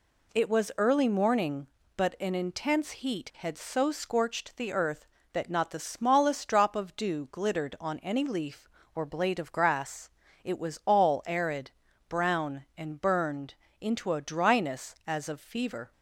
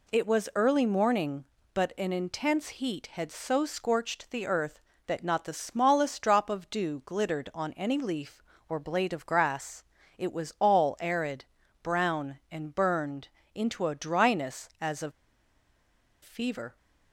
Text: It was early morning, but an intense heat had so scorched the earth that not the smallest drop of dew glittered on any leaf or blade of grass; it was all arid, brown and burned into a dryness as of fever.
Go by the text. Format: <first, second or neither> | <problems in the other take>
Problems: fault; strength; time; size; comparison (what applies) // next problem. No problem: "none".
first | pauses between "burned" and "into"; slight; at 13.2 s; 0.26 s long; slight in the first // pauses between "of" and "fever"; at 15.1 s; 1.1 s long